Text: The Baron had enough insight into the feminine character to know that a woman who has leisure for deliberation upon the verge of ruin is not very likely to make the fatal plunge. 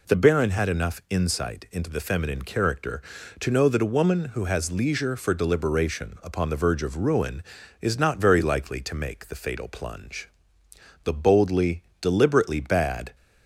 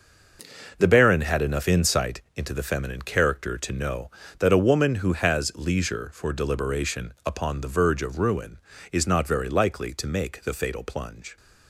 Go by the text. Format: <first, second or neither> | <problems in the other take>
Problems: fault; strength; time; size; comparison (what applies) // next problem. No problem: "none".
second | goes on to say "The boldly deliberately bad"; strong; from 11.0 s on; 2.1 s long